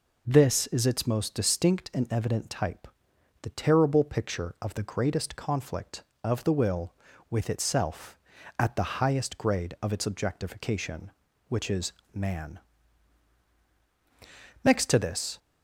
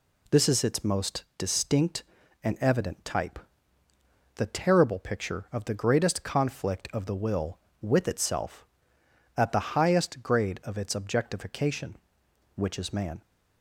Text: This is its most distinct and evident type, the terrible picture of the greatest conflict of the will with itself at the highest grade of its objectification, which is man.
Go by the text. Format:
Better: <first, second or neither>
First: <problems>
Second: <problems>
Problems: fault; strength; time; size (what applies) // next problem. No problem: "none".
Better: second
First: pauses between "is" and "man"; slight; at 11.9 s; 0.24 s long // goes on to say "Next to this"; noticeable; from 14.6 s on; 0.74 s long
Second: none